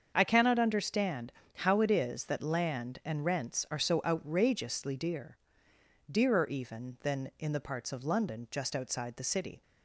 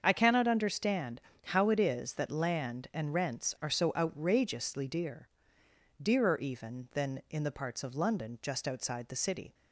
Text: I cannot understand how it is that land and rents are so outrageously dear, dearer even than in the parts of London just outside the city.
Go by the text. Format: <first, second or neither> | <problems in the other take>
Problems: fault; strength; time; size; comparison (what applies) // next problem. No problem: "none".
neither | starts louder than the rest; the same in both // pauses between "understand" and "how"; slight; the same in both